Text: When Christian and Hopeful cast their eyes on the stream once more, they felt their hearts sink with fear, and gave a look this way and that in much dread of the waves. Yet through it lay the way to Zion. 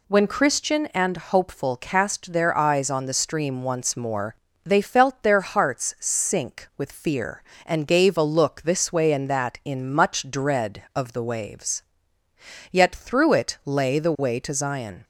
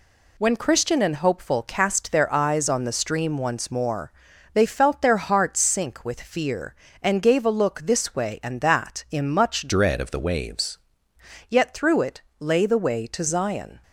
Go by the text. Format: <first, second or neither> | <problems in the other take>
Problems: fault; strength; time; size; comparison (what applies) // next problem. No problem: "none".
first | changes voice from "dread" to "waves"; from 9.6 to 10.7 s; 1.1 s long // pauses between "it" and "lay"; slight; at 12.2 s; 0.18 s long